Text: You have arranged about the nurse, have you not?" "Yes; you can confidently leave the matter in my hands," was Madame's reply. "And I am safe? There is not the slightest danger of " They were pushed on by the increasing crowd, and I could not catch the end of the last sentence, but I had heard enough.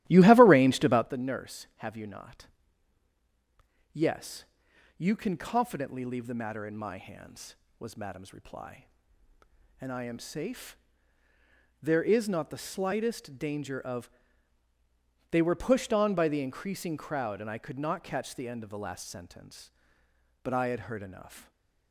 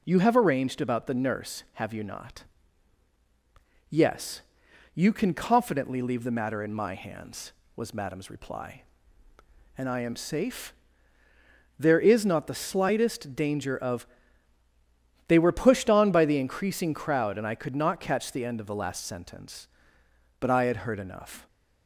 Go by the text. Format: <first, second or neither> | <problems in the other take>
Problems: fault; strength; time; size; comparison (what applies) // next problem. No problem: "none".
second | starts louder than the rest; strong; until 1.2 s; 14.5 dB